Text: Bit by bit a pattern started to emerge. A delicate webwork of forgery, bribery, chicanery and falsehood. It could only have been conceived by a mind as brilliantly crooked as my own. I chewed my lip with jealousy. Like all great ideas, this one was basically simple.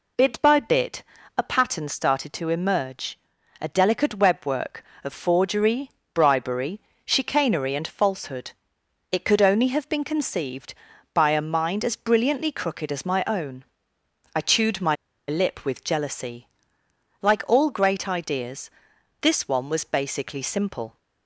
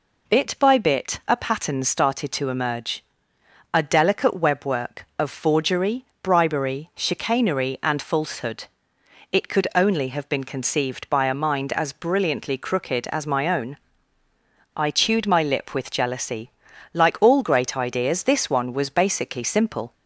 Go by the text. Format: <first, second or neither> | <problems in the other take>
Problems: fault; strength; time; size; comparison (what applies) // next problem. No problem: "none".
second | pauses between "bit" and "a"; slight; at 1.0 s; 0.32 s long // pauses between "my" and "lip"; slight; at 14.9 s; 0.32 s long